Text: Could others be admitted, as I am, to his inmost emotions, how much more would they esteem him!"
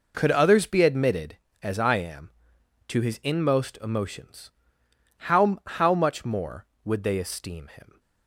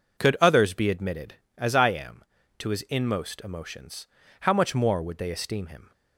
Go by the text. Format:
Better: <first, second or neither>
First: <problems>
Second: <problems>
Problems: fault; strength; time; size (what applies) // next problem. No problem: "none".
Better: second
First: says "how" twice; at 5.6 s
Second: none